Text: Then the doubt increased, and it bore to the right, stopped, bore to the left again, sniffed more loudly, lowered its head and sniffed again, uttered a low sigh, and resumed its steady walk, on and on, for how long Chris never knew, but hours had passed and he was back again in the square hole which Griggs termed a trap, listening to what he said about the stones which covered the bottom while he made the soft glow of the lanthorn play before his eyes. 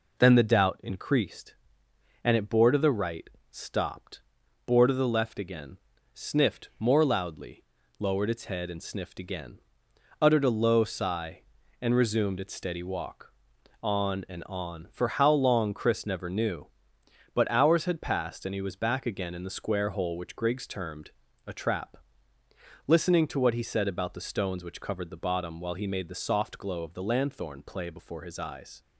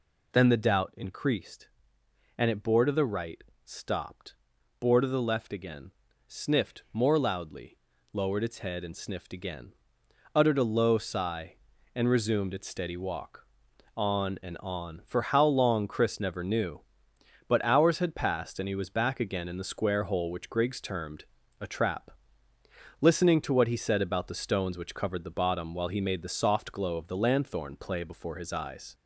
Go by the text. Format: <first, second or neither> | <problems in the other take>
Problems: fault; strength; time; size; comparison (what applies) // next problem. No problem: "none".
first | gets louder; slight; throughout; 2 dB // pauses between "termed" and "a"; slight; at 21.2 s; 0.36 s long; slight in the first